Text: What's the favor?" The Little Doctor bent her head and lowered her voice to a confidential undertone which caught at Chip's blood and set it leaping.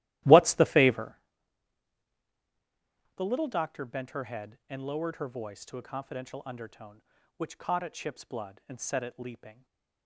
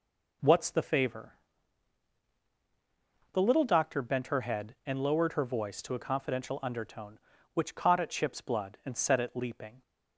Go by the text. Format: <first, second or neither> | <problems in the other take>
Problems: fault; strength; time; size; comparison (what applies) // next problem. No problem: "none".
second | starts louder than the rest; strong; until 1.2 s; 15.5 dB // stays silent after the last word; slight; from 9.5 s on; 0.5 s long